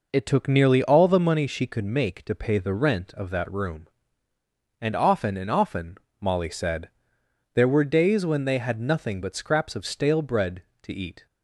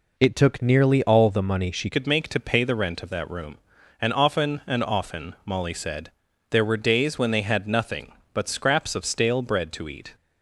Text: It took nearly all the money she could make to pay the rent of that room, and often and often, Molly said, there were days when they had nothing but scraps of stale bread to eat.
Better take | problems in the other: first | changes voice at "could"; from 1.9 s on; 8.2 s long

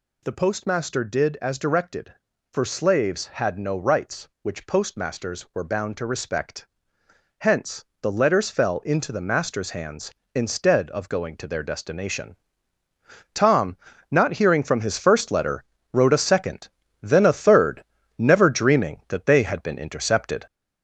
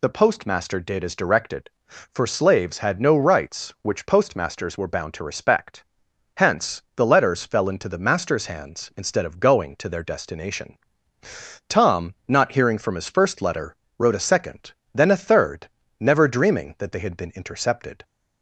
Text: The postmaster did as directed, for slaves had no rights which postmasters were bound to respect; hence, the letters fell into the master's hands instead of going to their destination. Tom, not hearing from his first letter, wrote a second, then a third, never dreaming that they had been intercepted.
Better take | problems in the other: second | gets louder; noticeable; throughout; 4.5 dB

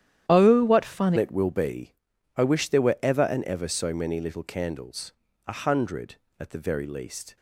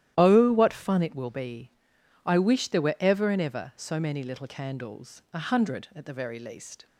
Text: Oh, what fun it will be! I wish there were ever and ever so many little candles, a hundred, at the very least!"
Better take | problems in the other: second | starts louder than the rest; strong; until 1.3 s; 11 dB; strong in the second // changes voice at "it"; from 1.1 s on; 6.2 s long

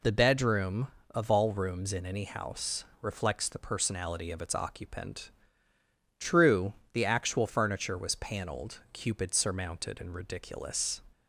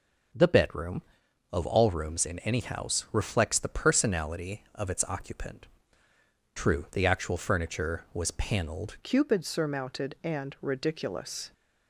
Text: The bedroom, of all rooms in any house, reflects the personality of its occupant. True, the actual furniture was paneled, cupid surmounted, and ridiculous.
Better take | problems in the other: first | starts louder than the rest; noticeable; until 1.8 s; 6 dB // changes voice at "cupid"; from 9.0 s on; 2.5 s long

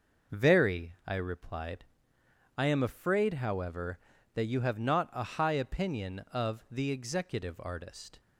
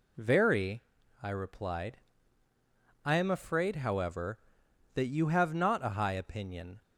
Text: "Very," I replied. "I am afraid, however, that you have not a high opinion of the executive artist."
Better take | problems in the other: first | stops before "of the executive artist"; at 6.8 s

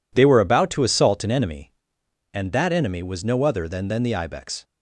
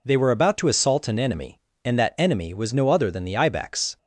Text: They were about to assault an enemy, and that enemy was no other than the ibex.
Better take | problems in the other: second | says "than" twice; at 3.8 s

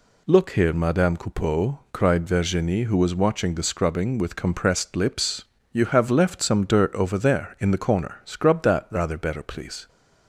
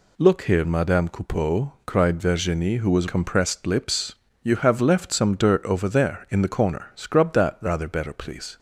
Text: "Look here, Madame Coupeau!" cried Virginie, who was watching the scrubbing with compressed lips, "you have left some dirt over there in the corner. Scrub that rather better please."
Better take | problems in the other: first | skips "watching the scrubbing with"; at 3.0 s

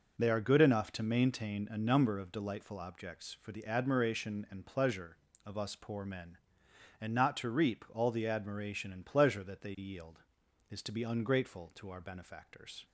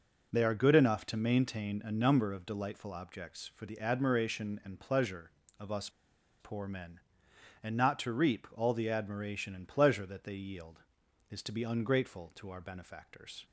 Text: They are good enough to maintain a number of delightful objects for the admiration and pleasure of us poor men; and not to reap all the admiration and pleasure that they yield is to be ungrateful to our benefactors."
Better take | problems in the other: first | pauses between "us" and "poor"; noticeable; at 5.8 s; 0.51 s long

